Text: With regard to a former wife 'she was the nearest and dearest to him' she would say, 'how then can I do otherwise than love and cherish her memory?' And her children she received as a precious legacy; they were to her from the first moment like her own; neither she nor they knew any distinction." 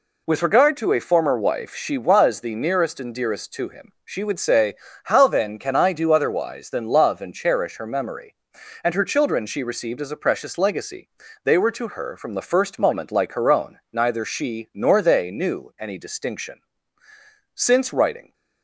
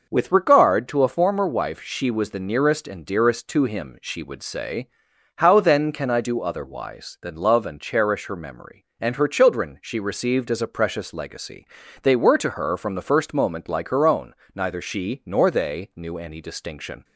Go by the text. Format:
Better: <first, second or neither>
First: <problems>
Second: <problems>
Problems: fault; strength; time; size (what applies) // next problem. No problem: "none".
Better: second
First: goes on to say "Since writing"; noticeable; from 17.5 s on; 0.80 s long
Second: none